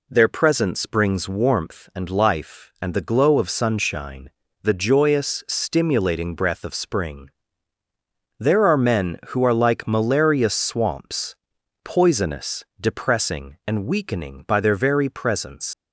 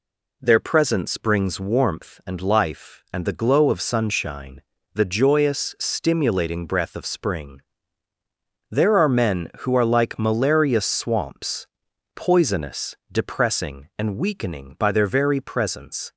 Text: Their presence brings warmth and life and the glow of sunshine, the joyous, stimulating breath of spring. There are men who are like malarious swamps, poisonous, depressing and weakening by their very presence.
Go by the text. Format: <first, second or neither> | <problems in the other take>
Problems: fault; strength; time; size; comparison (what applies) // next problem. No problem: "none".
second | leaves "presence" unfinished; at 15.7 s; 85 ms